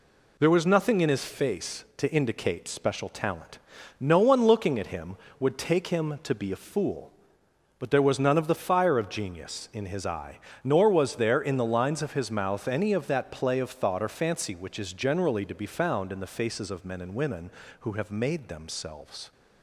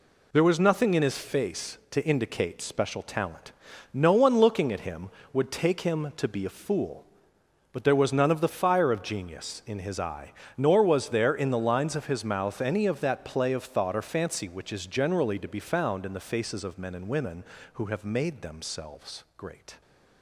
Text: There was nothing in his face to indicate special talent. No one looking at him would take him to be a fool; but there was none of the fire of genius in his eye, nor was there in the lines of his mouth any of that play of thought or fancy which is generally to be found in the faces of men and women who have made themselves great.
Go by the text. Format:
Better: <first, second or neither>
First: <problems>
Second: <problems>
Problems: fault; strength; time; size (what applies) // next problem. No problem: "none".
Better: second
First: stops before "great"; at 19.3 s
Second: none